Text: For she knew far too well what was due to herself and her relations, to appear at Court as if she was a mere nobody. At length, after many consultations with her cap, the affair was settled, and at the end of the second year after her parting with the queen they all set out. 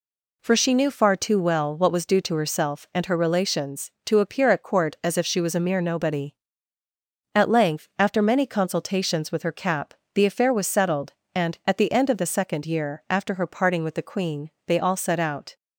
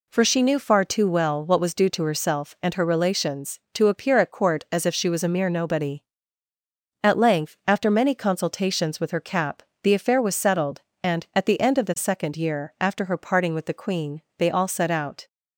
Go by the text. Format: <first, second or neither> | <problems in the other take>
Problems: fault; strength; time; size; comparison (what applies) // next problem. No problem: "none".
neither | pauses between "queen" and "they"; slight; the same in both